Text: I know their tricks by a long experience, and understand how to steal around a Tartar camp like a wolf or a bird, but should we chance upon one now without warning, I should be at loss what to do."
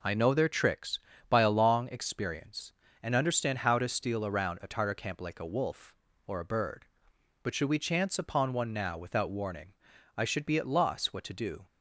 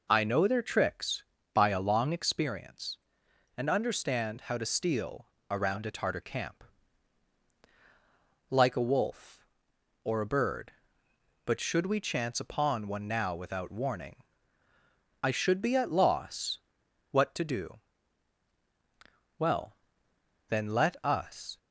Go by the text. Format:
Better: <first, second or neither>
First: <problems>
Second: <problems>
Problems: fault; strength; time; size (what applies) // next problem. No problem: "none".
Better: first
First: none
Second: pauses between "steal" and "around"; slight; at 5.2 s; 0.24 s long // pauses between "camp" and "like"; strong; at 6.6 s; 1.8 s long // pauses between "loss" and "what"; noticeable; at 16.5 s; 0.52 s long // goes on to say "Well then let us"; strong; from 19.3 s on; 2.1 s long